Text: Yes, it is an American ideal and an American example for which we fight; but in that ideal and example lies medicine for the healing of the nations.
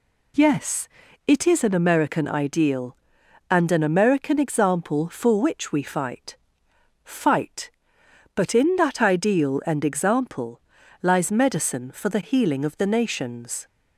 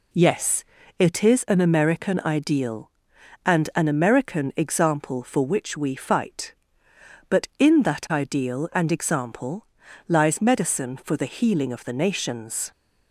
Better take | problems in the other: second | says "fight" twice; at 7.0 s // pauses between "example" and "lies"; at 10.5 s; 0.42 s long; also in the second

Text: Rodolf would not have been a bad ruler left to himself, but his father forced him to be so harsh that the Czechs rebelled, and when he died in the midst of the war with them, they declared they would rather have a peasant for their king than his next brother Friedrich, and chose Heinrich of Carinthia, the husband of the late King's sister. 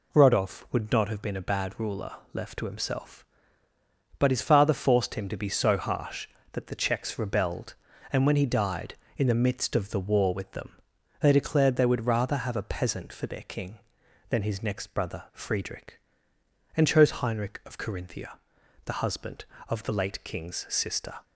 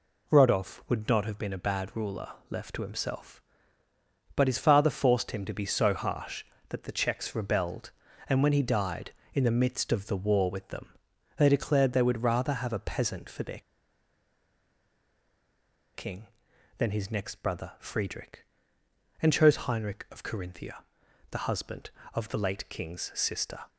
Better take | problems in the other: first | pauses between "ruler" and "left"; slight; at 2.3 s; 0.16 s long; slight in the first // pauses between "their" and "king"; strong; at 13.6 s; 2.3 s long

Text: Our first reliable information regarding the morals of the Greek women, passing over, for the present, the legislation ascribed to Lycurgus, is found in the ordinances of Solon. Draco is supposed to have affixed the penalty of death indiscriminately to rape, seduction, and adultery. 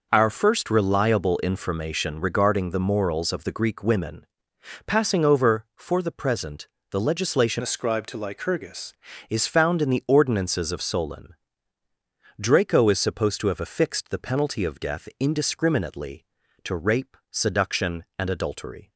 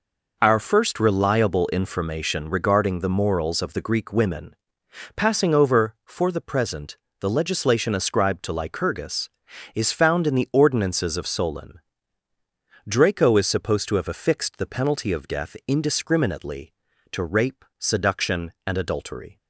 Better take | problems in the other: second | changes voice from "ascribed" to "Lycurgus"; from 7.6 to 8.9 s; 1.3 s long

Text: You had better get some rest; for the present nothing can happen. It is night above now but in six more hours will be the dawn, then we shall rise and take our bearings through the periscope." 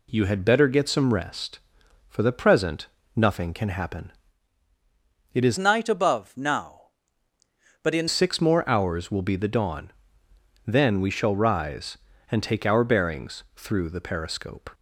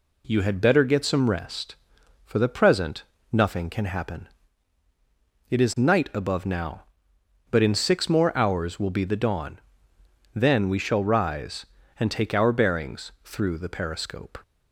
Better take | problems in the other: second | pauses between "present" and "nothing"; slight; at 2.8 s; 0.28 s long; slight in the second // changes voice from "night" to "in"; from 5.5 to 8.0 s; 2.5 s long

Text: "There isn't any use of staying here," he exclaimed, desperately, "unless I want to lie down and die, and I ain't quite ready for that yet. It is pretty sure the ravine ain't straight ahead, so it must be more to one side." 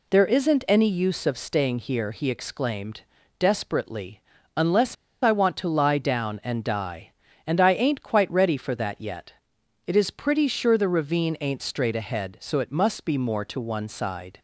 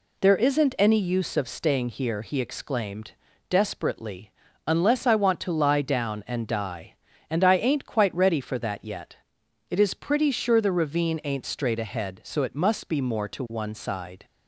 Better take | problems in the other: second | pauses between "unless" and "I"; slight; at 4.9 s; 0.27 s long

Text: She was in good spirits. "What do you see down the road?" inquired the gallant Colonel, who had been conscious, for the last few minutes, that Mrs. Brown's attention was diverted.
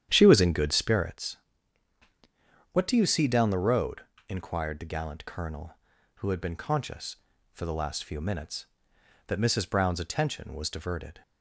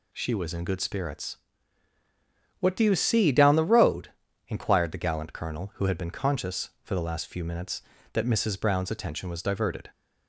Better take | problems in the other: second | starts louder than the rest; strong; until 1.2 s; 10 dB

